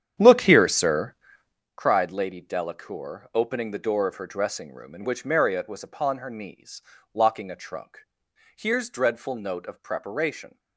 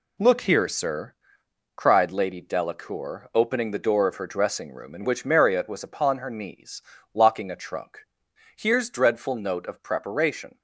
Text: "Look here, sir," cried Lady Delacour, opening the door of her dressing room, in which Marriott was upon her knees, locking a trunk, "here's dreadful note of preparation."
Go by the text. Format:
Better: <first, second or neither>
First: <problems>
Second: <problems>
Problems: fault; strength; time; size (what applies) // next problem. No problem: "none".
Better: second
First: starts louder than the rest; strong; until 1.6 s; 9 dB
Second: none